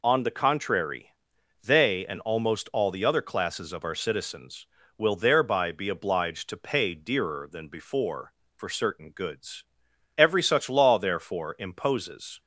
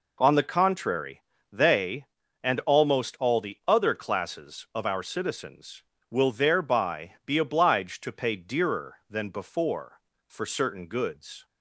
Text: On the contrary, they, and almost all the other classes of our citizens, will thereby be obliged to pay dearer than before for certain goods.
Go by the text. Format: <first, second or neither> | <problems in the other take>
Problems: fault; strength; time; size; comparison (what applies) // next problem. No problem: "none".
second | goes on to say "Every such law therefore imposes"; strong; from 10.1 s on; 2.2 s long